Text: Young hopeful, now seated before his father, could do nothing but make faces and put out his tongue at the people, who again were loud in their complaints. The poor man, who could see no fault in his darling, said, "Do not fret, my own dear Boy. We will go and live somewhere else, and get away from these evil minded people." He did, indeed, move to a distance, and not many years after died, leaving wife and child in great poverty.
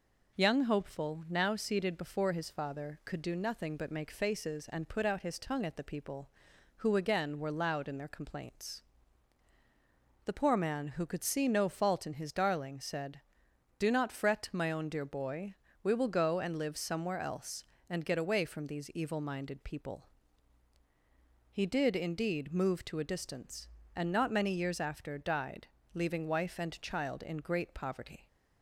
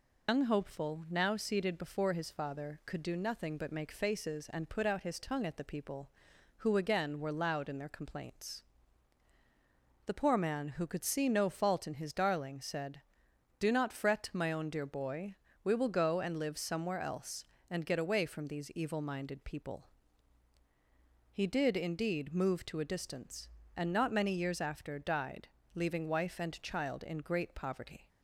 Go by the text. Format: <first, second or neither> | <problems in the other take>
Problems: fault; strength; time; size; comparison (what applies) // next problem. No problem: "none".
first | loses the start of "Young"; at 0.2 s; 125 ms